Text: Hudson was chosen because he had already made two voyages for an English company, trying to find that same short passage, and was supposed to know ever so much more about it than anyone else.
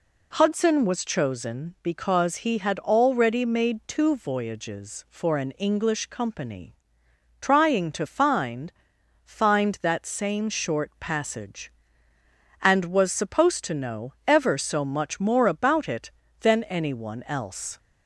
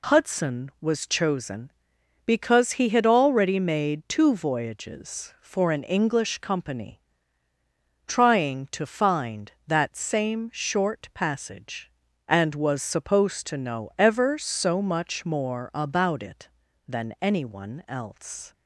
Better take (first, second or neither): second